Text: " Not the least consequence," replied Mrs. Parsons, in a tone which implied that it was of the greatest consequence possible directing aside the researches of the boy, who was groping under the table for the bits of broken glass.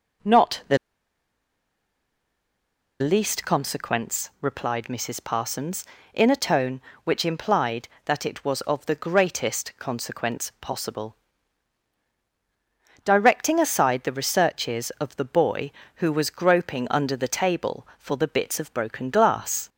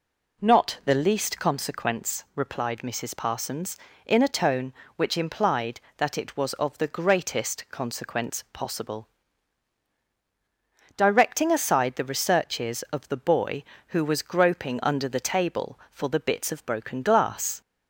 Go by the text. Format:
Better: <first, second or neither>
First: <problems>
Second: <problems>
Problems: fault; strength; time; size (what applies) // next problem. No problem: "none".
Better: second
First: pauses between "the" and "least"; strong; at 0.7 s; 2.2 s long // pauses between "possible" and "directing"; strong; at 11.1 s; 1.9 s long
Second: pauses between "possible" and "directing"; strong; at 9.0 s; 1.9 s long